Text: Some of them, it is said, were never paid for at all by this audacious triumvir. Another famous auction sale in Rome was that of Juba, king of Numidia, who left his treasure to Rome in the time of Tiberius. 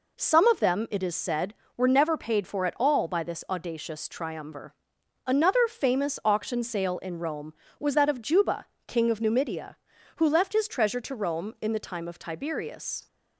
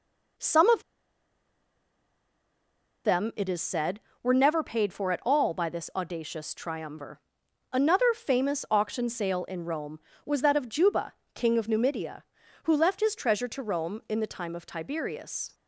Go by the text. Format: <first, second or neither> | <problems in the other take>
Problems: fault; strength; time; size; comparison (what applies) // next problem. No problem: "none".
first | pauses between "of" and "them"; strong; at 0.8 s; 2.2 s long